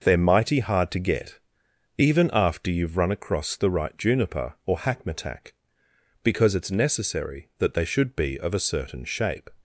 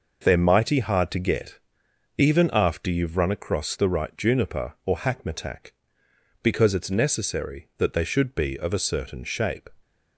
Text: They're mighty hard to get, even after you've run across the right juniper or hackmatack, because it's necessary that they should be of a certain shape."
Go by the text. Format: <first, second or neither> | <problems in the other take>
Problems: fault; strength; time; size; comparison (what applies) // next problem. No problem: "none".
neither | none